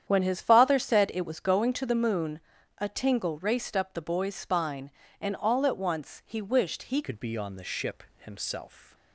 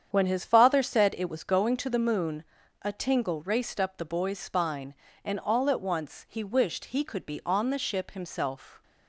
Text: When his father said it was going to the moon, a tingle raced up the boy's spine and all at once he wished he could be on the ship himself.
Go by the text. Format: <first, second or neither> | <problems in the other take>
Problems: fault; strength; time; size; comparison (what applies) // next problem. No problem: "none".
second | starts louder than the rest; strong; until 1.0 s; 9 dB; strong in the second // changes voice at "could"; from 7.0 s on; 1.9 s long // pauses between "ship" and "himself"; slight; at 8.0 s; 0.16 s long